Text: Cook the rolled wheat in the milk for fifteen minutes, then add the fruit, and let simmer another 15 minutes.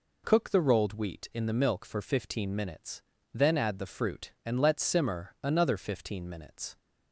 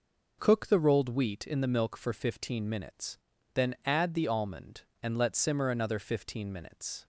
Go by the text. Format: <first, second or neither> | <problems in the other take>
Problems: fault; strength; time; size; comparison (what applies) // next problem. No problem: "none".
first | says "almond" for "fruit"; at 4.2 s